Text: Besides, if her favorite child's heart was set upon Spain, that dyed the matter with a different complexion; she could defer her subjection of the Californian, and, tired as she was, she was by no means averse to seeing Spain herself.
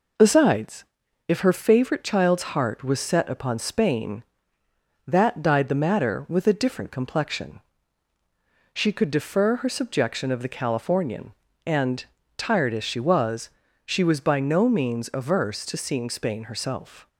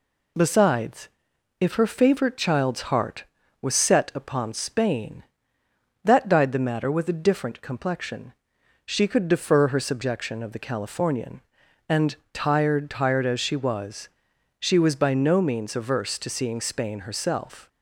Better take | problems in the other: first | says "tired" twice; at 12.8 s

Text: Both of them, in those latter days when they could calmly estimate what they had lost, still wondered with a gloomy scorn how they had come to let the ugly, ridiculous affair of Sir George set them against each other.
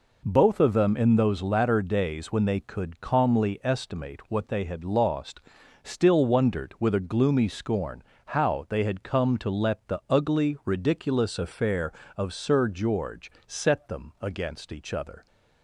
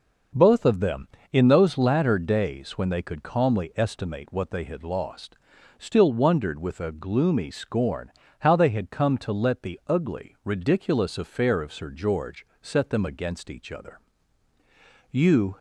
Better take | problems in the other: first | pauses between "scorn" and "how"; slight; at 8.0 s; 0.30 s long; slight in the first // pauses between "George" and "set"; slight; at 12.4 s; 0.16 s long; slight in the first // goes on to say "You"; slight; from 15.1 s on; 0.46 s long

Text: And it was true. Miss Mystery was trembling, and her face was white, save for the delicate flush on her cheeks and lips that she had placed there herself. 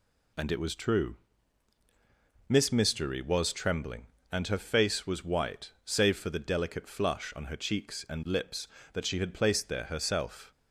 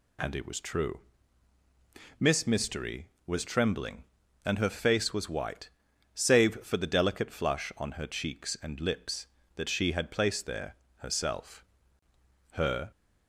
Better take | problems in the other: first | pauses between "there" and "herself"; slight; at 10.7 s; 0.20 s long // goes on to say "Her"; slight; from 12.5 s on; 0.38 s long

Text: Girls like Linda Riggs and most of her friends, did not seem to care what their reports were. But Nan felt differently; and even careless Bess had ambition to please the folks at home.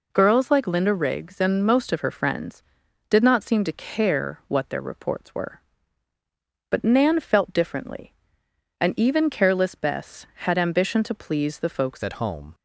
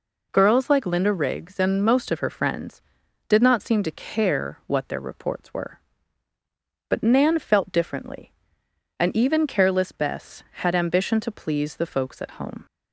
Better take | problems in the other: second | changes voice at "at"; from 12.0 s on; 0.5 s long

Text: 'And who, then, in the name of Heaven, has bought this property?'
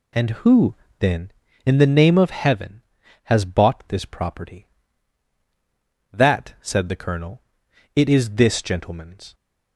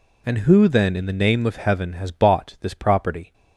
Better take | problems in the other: second | goes on to say "That said the Colonel it is this gentleman's"; strong; from 6.1 s on; 3.2 s long

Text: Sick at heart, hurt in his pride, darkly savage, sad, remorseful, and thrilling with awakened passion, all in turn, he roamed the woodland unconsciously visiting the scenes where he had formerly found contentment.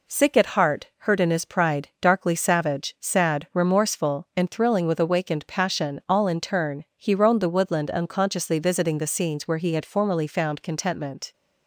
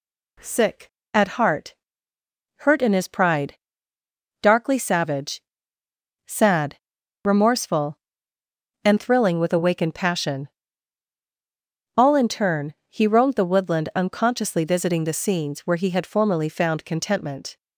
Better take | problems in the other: neither | none

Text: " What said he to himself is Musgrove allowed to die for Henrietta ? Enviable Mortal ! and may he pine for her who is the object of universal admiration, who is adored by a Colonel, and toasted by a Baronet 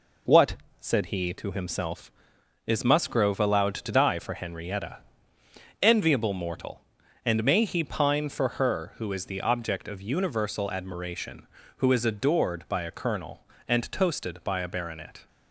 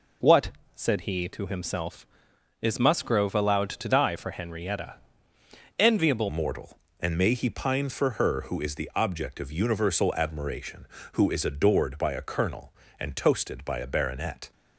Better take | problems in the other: first | pauses between "What" and "said"; slight; at 0.5 s; 0.24 s long; slight in the first // changes voice at "Mortal"; from 6.2 s on; 8.3 s long

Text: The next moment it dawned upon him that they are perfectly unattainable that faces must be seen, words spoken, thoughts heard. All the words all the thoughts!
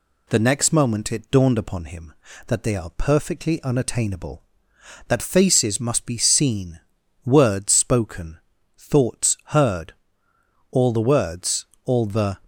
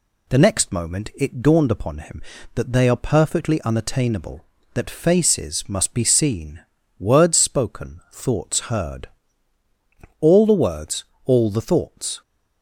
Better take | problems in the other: second | pauses between "words" and "all"; slight; at 11.6 s; 0.20 s long; slight in the second // stops before "thoughts"; at 12.4 s

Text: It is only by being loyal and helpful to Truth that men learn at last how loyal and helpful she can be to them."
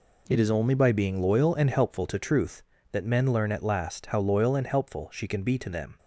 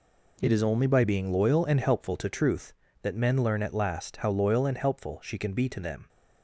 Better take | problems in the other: neither | none

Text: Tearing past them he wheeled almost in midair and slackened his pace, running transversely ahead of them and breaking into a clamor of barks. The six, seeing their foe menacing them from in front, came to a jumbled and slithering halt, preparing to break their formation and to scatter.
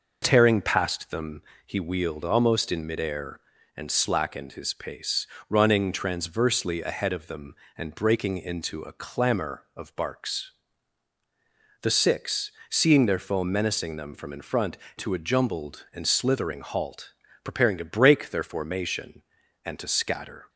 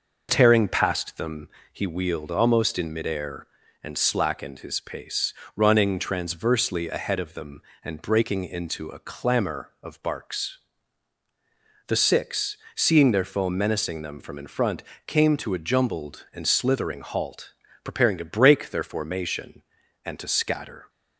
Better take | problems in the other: second | pauses between "them" and "he"; slight; at 1.4 s; 0.24 s long; slight in the second // skips "came"; at 14.8 s

